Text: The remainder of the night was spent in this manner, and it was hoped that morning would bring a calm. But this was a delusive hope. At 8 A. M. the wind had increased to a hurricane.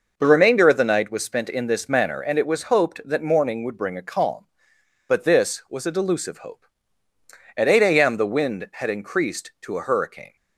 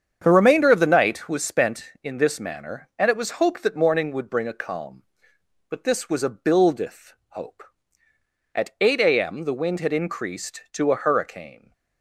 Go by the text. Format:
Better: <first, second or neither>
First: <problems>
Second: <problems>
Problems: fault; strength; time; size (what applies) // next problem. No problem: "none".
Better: first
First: none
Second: starts louder than the rest; strong; until 1.2 s; 7.5 dB // says "buildeth" for "delusive"; at 6.2 s